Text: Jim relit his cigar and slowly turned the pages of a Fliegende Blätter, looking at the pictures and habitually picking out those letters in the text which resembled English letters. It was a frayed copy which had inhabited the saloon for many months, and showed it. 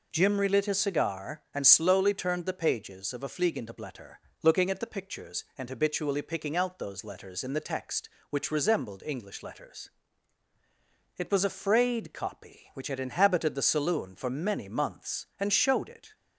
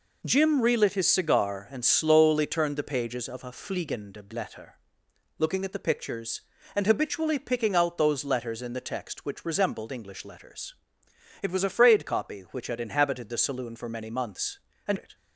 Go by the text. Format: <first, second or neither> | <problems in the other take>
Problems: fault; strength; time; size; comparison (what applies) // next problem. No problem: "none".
first | skips "showed"; at 14.9 s